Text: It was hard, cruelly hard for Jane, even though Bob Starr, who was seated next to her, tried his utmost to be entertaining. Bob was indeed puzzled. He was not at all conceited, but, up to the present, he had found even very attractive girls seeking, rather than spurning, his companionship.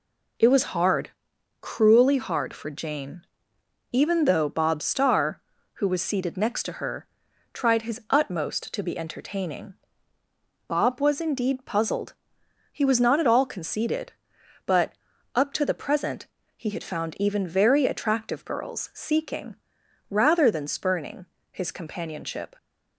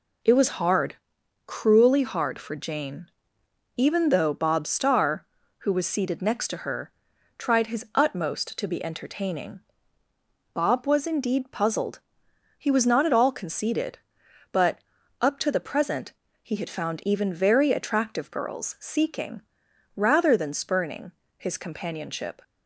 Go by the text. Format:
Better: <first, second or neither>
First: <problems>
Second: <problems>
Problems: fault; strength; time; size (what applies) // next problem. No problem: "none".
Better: neither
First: none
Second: none